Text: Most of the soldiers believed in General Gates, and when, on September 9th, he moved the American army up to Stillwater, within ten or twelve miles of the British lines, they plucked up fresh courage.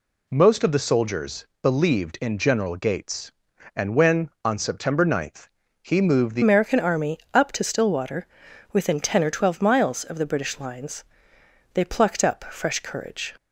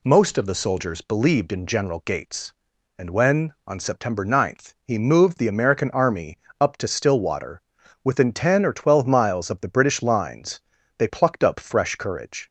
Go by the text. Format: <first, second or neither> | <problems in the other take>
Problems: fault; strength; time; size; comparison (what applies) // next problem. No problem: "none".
second | pauses between "soldiers" and "believed"; slight; at 1.4 s; 0.16 s long // changes voice at "American"; from 6.4 s on; 6.9 s long // pauses between "army" and "up"; slight; at 7.1 s; 0.16 s long; slight in the second